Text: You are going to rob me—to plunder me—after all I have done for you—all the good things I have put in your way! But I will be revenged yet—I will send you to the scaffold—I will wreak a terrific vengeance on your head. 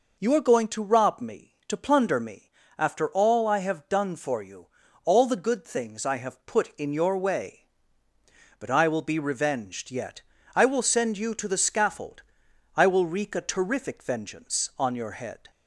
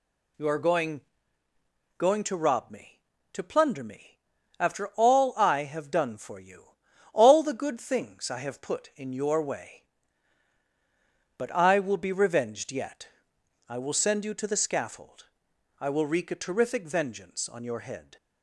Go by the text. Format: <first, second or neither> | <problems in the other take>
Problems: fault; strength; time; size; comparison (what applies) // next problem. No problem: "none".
first | says "going" twice; at 1.9 s